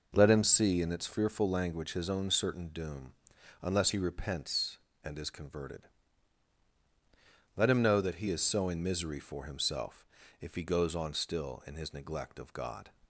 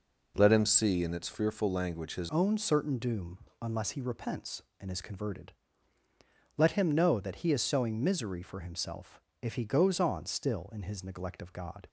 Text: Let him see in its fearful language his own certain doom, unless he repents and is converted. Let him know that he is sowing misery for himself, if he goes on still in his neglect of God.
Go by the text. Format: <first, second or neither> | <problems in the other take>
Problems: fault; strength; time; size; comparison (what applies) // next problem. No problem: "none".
first | changes voice at "own"; from 2.3 s on; 9.5 s long